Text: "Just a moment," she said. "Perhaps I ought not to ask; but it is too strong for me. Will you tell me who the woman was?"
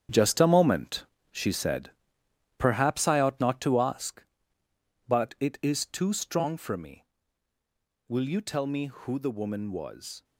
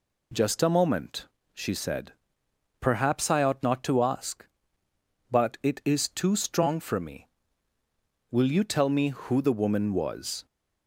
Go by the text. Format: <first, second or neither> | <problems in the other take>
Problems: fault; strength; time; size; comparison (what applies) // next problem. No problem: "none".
second | gets quieter; strong; throughout; 9.5 dB